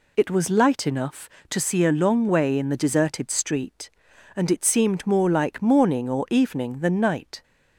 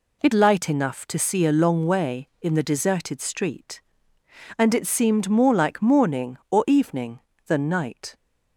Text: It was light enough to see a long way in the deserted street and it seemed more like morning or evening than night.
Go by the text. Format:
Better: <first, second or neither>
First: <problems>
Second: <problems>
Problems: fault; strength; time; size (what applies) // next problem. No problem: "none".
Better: first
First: none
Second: skips "was"; at 0.3 s